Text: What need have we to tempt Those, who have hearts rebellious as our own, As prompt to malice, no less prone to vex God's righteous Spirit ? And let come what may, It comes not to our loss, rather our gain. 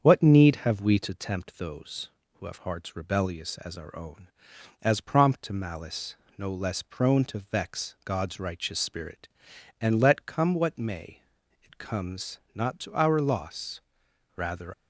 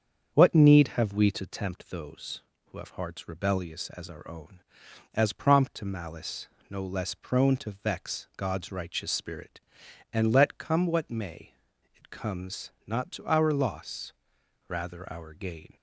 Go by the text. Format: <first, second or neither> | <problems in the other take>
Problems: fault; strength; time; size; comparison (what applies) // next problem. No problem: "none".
second | starts louder than the rest; strong; until 1.0 s; 7.5 dB; strong in the second // pauses between "comes" and "not"; slight; at 12.3 s; 0.16 s long; slight in the second // stops before "our gain"; at 14.7 s